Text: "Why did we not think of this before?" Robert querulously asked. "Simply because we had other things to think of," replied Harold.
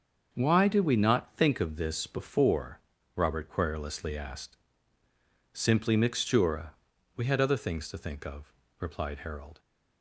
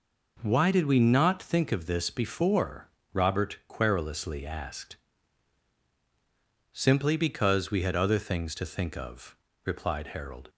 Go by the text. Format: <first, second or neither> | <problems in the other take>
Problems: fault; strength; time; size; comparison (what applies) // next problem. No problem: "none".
second | starts louder than the rest; until 1.3 s; 6.5 dB // says "mixtura" for "because"; at 5.9 s